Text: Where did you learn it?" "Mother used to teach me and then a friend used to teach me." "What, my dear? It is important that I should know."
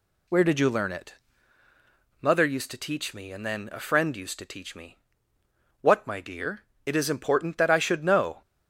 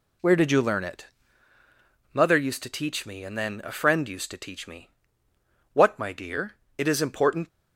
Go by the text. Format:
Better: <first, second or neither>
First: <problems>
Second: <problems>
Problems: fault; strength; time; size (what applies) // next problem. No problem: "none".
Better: first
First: none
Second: stops before "that I should know"; at 7.4 s